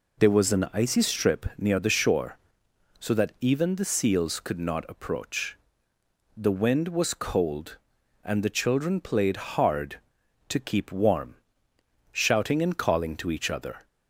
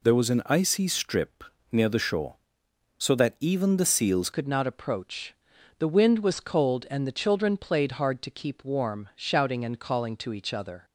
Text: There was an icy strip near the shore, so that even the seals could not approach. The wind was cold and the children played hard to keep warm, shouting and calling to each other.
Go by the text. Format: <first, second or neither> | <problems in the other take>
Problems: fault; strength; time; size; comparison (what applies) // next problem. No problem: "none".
first | pauses between "strip" and "near"; slight; at 1.4 s; 0.26 s long // changes voice at "could"; from 4.3 s on; 6.5 s long